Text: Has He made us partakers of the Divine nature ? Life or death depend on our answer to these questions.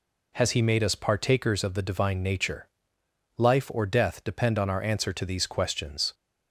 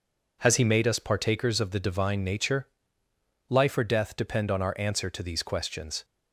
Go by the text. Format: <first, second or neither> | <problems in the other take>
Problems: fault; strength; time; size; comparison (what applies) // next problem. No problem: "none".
neither | none